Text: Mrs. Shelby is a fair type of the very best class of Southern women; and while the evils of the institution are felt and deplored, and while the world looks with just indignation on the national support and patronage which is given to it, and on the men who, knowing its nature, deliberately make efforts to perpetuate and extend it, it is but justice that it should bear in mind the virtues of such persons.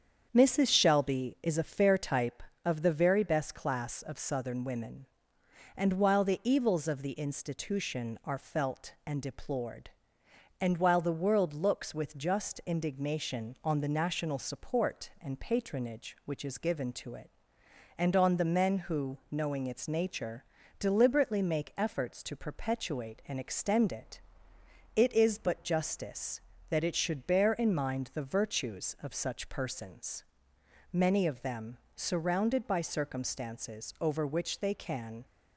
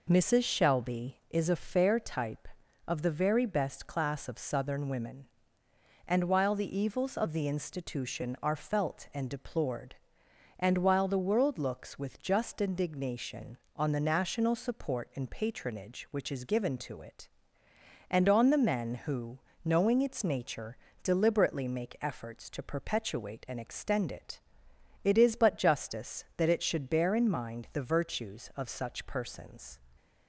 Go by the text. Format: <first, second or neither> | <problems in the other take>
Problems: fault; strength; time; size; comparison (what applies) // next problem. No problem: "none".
second | starts louder than the rest; strong; until 1.3 s; 7.5 dB // goes on to say "Many of them surrounded by circumstances over which they can"; strong; from 30.9 s on; 4.3 s long